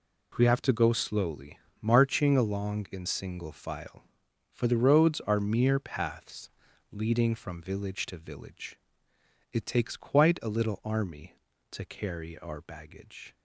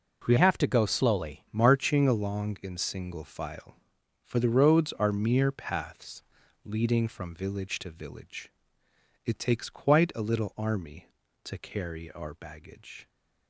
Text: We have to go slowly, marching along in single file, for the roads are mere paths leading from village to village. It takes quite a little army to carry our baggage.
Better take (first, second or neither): first